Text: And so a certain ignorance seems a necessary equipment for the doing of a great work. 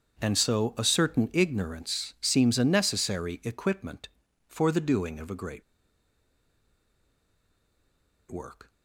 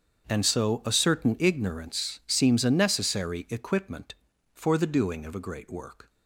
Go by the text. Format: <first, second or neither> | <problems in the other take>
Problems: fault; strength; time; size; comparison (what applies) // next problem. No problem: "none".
second | starts louder than the rest; strong; until 1.2 s; 7.5 dB; strong in the second // pauses between "great" and "work"; strong; at 5.6 s; 2.6 s long